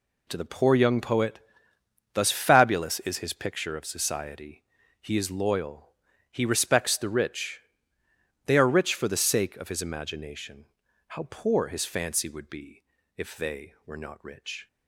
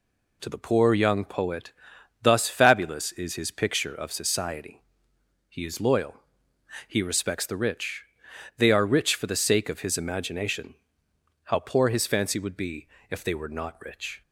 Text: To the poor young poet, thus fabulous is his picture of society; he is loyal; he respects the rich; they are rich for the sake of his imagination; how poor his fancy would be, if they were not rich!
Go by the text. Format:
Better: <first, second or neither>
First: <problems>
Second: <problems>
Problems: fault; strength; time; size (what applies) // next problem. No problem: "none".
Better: neither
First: none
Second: none